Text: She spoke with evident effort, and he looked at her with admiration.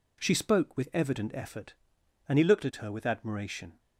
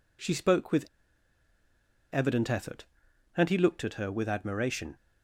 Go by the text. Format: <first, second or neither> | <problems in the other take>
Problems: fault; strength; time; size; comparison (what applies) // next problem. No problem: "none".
first | pauses between "with" and "evident"; strong; at 0.8 s; 1.2 s long